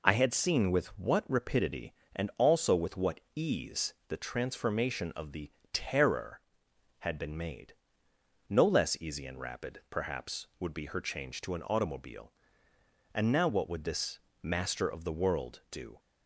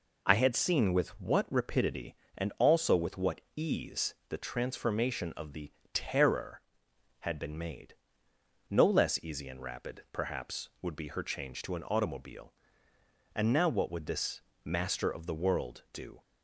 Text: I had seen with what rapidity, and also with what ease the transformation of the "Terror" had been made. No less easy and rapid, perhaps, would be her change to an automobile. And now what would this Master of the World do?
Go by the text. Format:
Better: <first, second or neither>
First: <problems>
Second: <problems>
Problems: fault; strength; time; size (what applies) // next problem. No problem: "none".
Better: neither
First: pauses between "what" and "ease"; slight; at 3.1 s; 0.16 s long // pauses between "the" and "Terror"; slight; at 5.5 s; 0.22 s long // pauses between "this" and "Master"; slight; at 14.1 s; 0.22 s long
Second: pauses between "what" and "ease"; slight; at 3.3 s; 0.16 s long // pauses between "the" and "Terror"; slight; at 5.7 s; 0.22 s long // pauses between "this" and "Master"; slight; at 14.4 s; 0.22 s long